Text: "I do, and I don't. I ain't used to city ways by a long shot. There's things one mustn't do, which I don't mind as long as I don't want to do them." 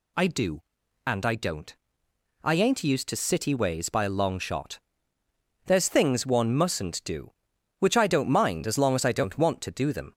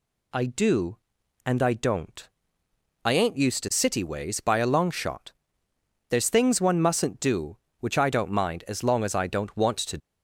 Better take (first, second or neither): first